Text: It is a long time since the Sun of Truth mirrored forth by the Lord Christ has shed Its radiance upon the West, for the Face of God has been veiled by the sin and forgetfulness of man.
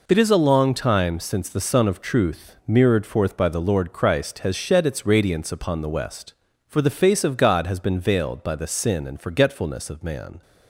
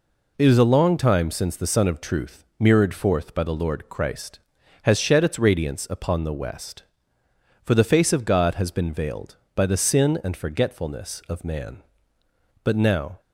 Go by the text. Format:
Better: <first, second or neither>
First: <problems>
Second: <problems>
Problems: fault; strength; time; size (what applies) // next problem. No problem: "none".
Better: first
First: none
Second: goes on to say "But now"; from 12.6 s on; 0.56 s long